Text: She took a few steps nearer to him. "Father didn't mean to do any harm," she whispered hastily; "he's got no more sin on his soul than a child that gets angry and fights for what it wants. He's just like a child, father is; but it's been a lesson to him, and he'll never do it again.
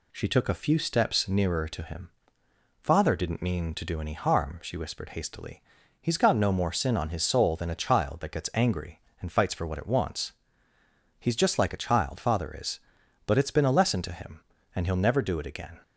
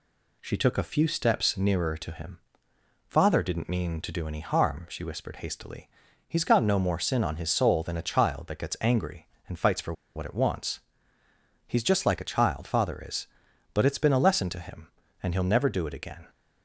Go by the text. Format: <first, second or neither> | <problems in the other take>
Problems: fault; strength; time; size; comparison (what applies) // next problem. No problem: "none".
first | pauses between "for" and "what"; slight; at 9.9 s; 0.23 s long